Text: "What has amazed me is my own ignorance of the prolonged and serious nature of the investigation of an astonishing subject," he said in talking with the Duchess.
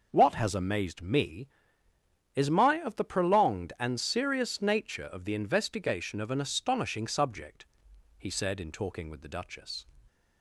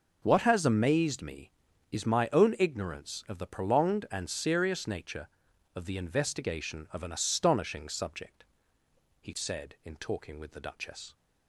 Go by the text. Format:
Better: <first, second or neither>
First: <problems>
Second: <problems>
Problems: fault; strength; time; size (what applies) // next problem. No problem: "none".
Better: second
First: skips "own ignorance"; at 2.8 s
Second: none